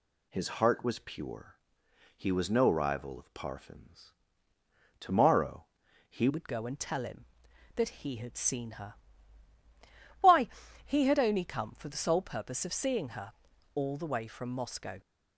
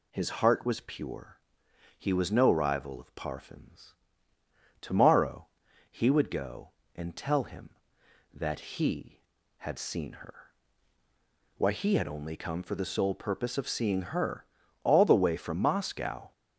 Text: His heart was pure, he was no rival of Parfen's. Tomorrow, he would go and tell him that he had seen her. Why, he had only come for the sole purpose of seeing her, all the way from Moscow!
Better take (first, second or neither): second